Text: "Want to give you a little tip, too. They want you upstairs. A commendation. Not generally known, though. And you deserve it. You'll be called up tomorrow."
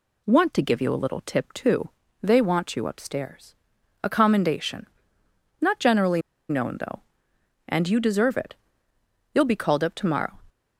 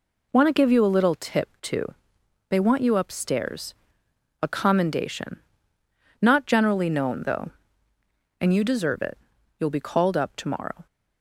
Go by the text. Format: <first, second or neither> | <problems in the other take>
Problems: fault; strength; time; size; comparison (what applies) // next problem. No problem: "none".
second | pauses between "generally" and "known"; slight; at 6.2 s; 0.28 s long